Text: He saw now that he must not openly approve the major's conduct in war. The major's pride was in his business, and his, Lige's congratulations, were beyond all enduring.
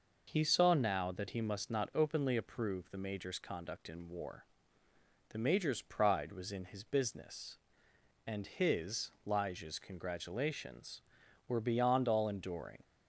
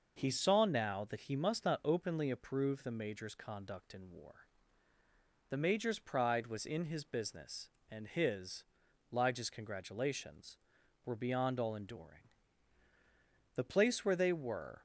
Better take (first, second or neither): first